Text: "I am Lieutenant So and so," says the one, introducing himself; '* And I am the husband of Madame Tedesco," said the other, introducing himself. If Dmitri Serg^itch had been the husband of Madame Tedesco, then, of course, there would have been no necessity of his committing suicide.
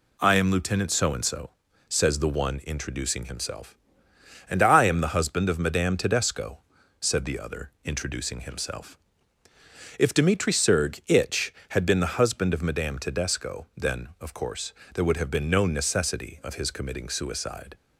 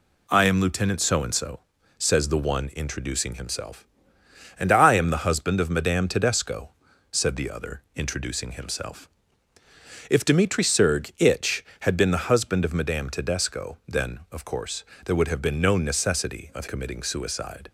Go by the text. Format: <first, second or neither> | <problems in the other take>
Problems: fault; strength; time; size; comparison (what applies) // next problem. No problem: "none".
first | skips "his"; at 16.6 s